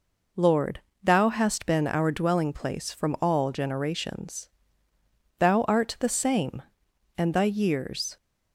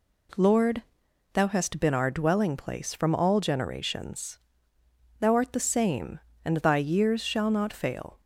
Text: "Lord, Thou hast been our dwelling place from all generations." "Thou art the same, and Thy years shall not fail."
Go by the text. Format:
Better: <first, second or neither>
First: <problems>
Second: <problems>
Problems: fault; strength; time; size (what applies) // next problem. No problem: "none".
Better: second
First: stops before "shall not fail"; at 8.1 s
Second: none